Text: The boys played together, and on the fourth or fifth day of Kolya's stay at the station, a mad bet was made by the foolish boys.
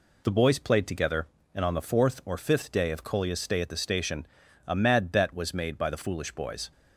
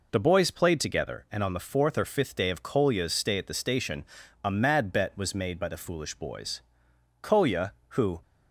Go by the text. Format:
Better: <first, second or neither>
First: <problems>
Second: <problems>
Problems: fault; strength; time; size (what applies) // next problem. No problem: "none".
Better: first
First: none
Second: goes on to say "Kolya who"; noticeable; from 7.2 s on; 1.0 s long